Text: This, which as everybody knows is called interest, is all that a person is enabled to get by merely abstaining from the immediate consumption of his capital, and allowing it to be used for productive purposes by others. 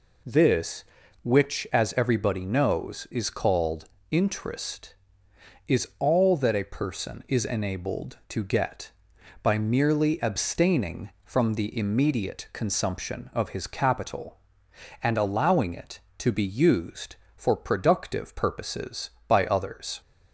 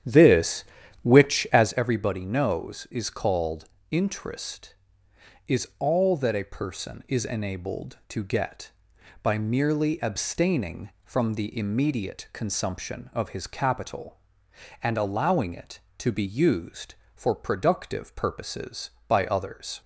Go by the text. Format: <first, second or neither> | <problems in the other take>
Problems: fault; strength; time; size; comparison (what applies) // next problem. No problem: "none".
first | starts louder than the rest; strong; until 1.8 s; 10 dB // pauses between "called" and "interest"; slight; at 3.6 s; 0.24 s long; slight in the first